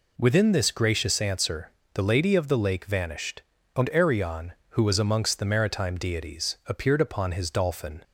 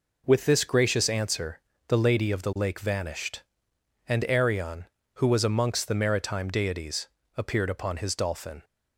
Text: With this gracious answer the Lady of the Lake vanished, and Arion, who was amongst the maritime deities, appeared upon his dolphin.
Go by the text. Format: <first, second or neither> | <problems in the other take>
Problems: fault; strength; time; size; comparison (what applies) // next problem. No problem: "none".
second | says "Within" for "With"; at 0.1 s // pauses between "answer" and "the"; slight; at 1.6 s; 0.23 s long; slight in the second